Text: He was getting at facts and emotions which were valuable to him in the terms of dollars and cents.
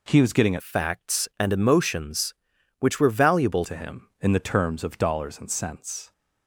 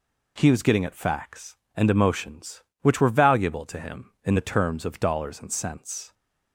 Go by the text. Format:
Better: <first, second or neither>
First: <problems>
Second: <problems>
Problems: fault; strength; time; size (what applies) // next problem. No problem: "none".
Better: second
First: changes voice from "facts" to "valuable"; from 0.6 to 3.6 s; 3.0 s long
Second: none